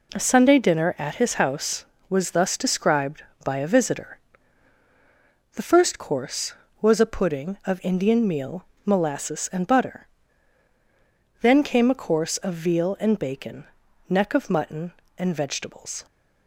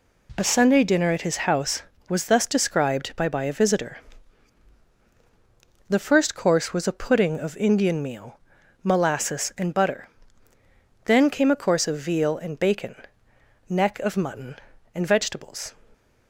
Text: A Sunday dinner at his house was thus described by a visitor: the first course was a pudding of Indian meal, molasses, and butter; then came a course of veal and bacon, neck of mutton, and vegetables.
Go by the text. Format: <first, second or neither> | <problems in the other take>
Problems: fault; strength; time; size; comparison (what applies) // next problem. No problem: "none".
first | says "by" twice; at 3.2 s